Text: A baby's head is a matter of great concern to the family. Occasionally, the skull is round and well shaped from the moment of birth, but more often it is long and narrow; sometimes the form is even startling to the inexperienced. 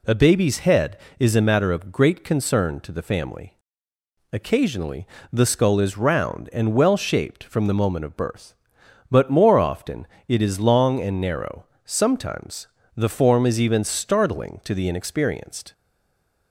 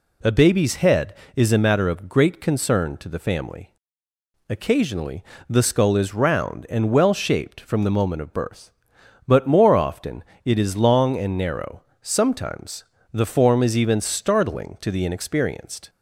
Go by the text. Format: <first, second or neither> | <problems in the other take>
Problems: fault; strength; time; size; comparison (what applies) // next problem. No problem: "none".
second | pauses between "often" and "it"; slight; at 10.0 s; 0.22 s long; slight in the second // pauses between "sometimes" and "the"; slight; at 12.6 s; 0.28 s long; slight in the second // stays silent after the last word; slight; from 15.7 s on; 0.8 s long